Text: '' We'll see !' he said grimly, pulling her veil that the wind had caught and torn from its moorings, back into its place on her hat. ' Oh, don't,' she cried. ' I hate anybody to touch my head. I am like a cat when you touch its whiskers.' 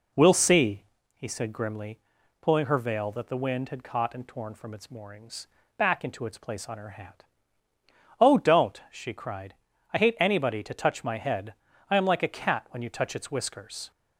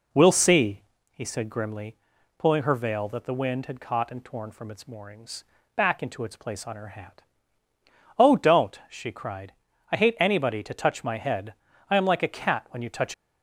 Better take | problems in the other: first | stops before "its whiskers"; at 13.1 s

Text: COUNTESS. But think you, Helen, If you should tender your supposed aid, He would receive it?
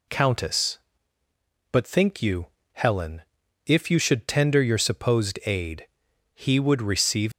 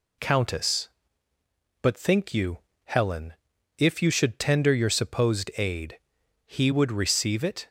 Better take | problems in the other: second | stops before "it"; at 7.3 s

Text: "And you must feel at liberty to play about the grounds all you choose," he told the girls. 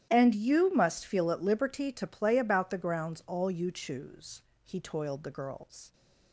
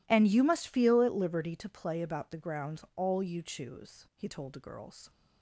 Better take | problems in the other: second | starts louder than the rest; strong; until 1.1 s; 11.5 dB // says "toiled" for "told"; at 4.8 s

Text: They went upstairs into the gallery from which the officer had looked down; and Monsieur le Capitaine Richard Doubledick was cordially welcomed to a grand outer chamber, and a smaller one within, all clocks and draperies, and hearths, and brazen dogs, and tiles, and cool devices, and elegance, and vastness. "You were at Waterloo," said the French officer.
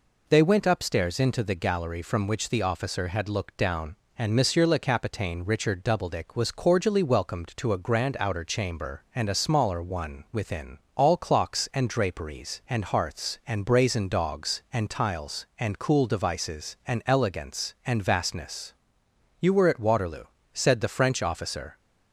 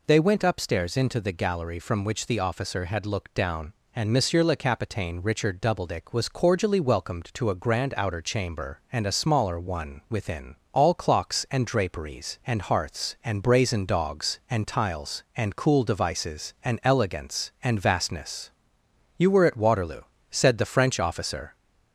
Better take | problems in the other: first | gets louder; slight; throughout; 2.5 dB

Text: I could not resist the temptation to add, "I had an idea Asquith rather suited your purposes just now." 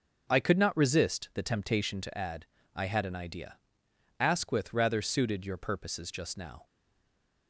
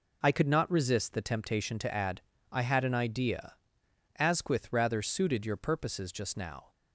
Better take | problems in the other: second | pauses between "idea" and "Asquith"; noticeable; at 3.5 s; 0.60 s long; noticeable in the second // stays silent after the last word; slight; from 6.6 s on; 0.8 s long

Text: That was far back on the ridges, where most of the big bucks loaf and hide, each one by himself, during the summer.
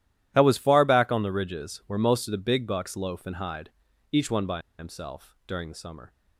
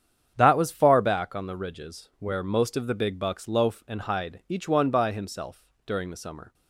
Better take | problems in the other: second | starts louder than the rest; strong; until 1.3 s; 12.5 dB; strong in the second // pauses between "by" and "himself"; slight; at 4.5 s; 0.19 s long

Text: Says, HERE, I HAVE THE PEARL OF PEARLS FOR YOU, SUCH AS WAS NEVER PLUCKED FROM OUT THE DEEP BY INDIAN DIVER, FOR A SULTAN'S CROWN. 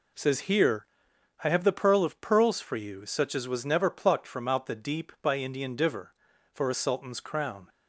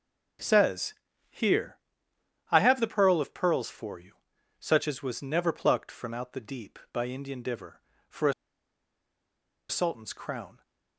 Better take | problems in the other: first | pauses between "A" and "SULTAN'S"; strong; at 8.3 s; 1.3 s long

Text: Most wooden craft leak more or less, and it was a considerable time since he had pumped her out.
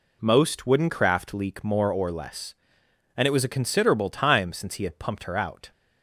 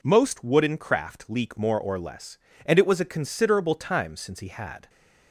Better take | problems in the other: first | stops before "pumped her out"; at 4.8 s

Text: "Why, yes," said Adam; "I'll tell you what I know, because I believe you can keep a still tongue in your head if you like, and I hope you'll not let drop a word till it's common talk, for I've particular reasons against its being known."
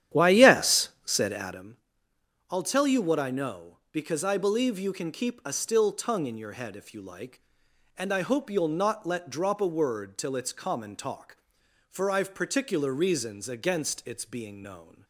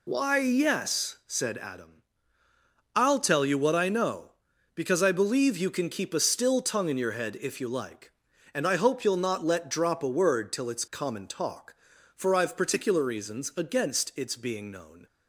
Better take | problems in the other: second | starts louder than the rest; strong; until 1.7 s; 10.5 dB

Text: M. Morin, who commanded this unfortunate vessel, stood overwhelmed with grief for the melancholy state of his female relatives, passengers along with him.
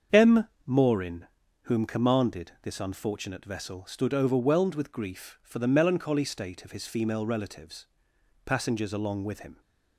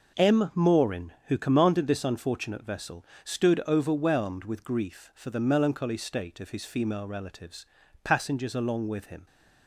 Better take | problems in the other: second | starts louder than the rest; until 1.6 s; 7 dB // says "whom" for "who"; at 1.6 s

